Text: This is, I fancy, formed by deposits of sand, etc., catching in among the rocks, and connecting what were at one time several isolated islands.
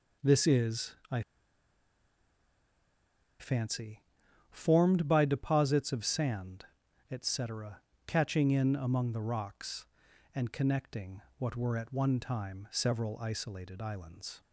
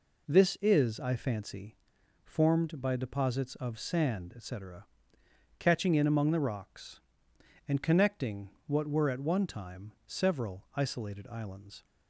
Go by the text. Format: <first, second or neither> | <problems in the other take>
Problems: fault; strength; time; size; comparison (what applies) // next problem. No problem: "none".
second | pauses between "I" and "fancy"; strong; at 1.2 s; 2.1 s long // pauses between "connecting" and "what"; slight; at 11.2 s; 0.18 s long; slight in the second